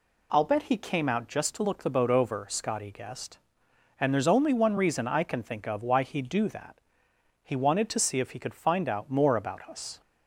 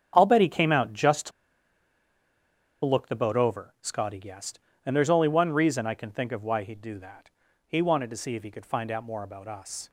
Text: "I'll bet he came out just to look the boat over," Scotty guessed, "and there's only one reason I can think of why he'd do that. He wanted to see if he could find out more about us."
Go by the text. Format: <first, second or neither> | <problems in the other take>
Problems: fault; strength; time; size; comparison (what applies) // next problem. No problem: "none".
first | starts louder than the rest; strong; until 1.1 s; 8 dB // pauses between "to" and "look"; strong; at 1.3 s; 1.5 s long